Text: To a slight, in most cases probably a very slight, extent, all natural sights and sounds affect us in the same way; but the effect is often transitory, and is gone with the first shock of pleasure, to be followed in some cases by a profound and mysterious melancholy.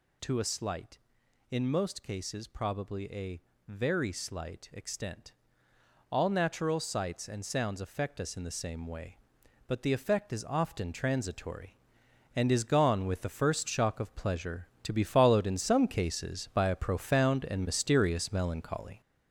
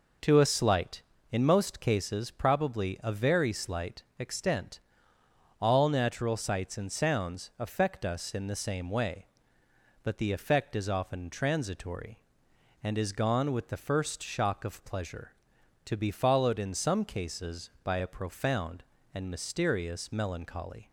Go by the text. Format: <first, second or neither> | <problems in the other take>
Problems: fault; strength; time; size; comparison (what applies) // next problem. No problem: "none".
second | gets louder; throughout; 6 dB // pauses between "a" and "very"; slight; at 3.3 s; 0.30 s long